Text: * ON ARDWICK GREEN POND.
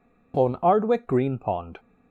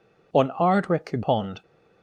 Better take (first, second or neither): first